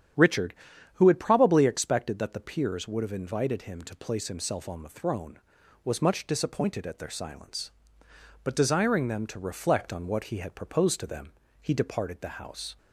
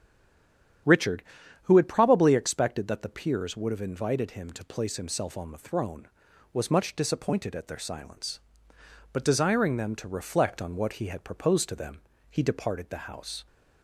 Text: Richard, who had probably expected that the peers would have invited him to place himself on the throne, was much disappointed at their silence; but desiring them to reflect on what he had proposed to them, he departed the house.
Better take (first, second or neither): first